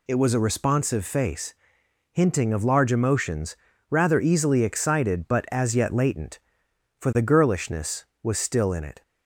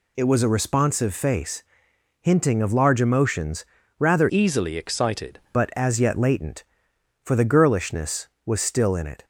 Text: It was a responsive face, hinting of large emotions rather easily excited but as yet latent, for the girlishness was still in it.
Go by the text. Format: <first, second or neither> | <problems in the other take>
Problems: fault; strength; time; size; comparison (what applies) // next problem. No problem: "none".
first | pauses between "emotions" and "rather"; slight; at 3.6 s; 0.34 s long; slight in the first // changes voice from "easily" to "excited"; from 4.2 to 5.3 s; 1.1 s long